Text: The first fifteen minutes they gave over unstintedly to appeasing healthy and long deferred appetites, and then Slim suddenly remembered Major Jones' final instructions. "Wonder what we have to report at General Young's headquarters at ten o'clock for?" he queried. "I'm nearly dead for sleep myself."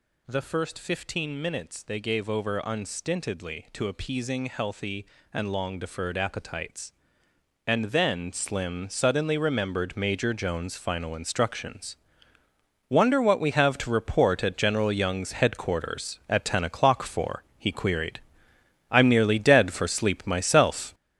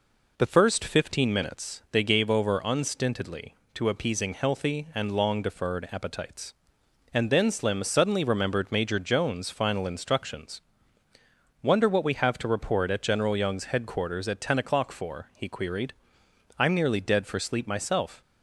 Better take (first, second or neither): second